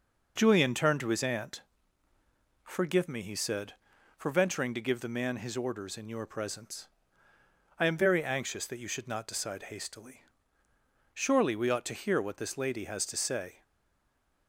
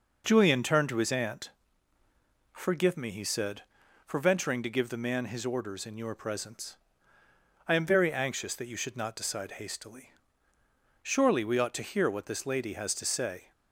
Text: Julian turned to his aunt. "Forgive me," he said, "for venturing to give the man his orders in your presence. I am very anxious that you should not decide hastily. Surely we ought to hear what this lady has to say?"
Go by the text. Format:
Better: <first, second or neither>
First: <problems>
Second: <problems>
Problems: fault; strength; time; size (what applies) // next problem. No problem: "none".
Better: second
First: stays silent after the last word; slight; from 13.6 s on; 0.8 s long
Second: none